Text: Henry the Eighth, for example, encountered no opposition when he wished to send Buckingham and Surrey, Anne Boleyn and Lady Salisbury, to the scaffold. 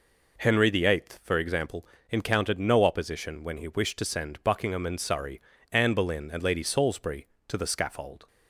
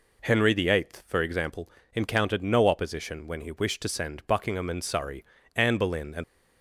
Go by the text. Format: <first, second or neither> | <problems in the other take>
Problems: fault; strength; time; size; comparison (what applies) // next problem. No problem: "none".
first | stops before "Lady Salisbury to the scaffold"; at 6.2 s